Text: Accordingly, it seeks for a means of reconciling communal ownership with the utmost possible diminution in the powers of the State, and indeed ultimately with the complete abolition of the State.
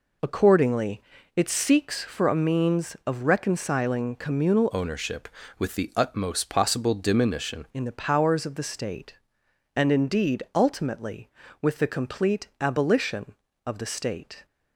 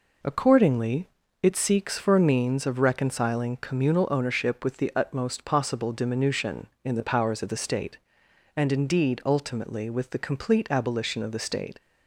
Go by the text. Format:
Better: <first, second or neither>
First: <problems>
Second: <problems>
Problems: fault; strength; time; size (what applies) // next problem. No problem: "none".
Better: second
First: changes voice from "ownership" to "diminution"; from 4.7 to 7.6 s; 2.9 s long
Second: none